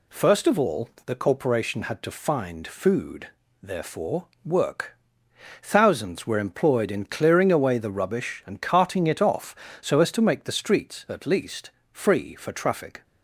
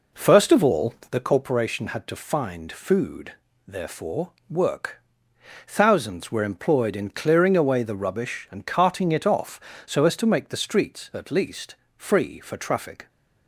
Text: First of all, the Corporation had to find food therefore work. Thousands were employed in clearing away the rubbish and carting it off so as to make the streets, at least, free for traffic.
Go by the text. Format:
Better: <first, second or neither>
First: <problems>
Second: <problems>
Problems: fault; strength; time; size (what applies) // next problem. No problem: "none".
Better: first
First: pauses between "food" and "therefore"; slight; at 3.2 s; 0.34 s long // pauses between "therefore" and "work"; slight; at 4.2 s; 0.16 s long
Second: starts louder than the rest; noticeable; until 1.5 s; 4.5 dB // pauses between "food" and "therefore"; slight; at 3.3 s; 0.34 s long // pauses between "therefore" and "work"; slight; at 4.3 s; 0.16 s long